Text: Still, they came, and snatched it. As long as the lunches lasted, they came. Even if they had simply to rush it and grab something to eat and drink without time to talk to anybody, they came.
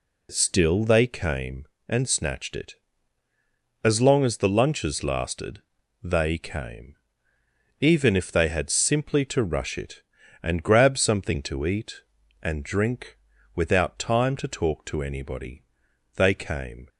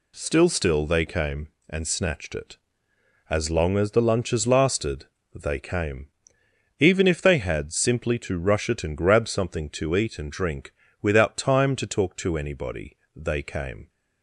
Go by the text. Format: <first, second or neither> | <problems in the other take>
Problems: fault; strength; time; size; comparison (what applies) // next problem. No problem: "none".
first | says "Still" twice; at 0.4 s // pauses between "drink" and "without"; slight; at 10.7 s; 0.32 s long; also in the first